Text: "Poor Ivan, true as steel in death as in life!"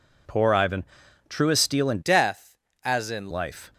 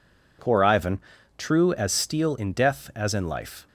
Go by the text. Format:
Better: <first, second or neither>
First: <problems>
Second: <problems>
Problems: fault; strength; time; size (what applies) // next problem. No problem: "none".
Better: second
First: changes voice from "death" to "in"; from 2.0 to 3.2 s; 1.2 s long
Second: none